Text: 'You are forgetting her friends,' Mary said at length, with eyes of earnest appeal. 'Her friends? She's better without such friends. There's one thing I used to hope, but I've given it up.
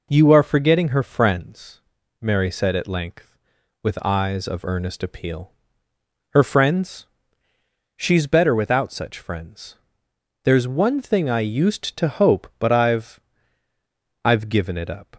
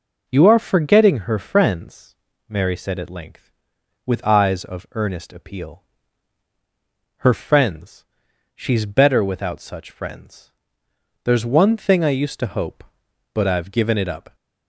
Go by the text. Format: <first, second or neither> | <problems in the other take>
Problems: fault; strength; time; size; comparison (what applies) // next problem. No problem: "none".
second | says "I've" twice; at 14.2 s